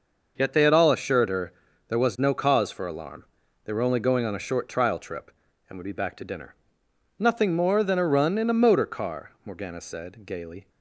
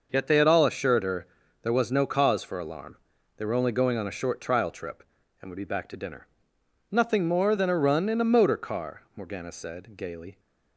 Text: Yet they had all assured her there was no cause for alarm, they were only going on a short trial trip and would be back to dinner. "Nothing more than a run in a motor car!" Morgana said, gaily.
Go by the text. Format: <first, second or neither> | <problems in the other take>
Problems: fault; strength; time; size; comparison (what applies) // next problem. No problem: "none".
neither | pauses between "her" and "there"; slight; the same in both